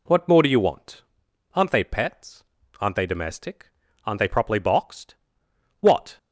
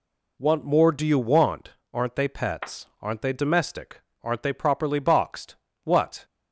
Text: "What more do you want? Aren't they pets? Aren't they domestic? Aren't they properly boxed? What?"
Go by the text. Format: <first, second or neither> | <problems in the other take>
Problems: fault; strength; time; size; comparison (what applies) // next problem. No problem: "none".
neither | none